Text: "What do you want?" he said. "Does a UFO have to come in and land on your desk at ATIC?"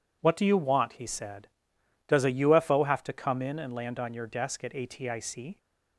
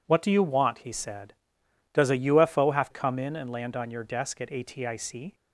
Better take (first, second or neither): first